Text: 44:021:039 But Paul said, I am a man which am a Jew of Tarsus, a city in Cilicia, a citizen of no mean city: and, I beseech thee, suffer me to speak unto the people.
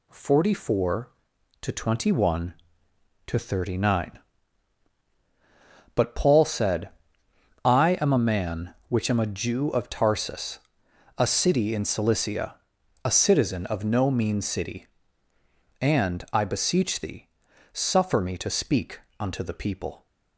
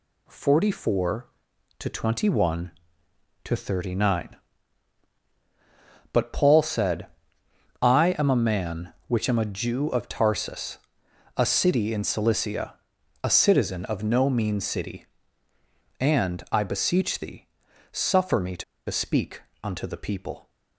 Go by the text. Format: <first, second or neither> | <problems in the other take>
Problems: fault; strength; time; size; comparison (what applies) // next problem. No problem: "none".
first | pauses between "to" and "speak"; slight; at 18.6 s; 0.25 s long // pauses between "speak" and "unto"; slight; at 19.4 s; 0.20 s long; slight in the first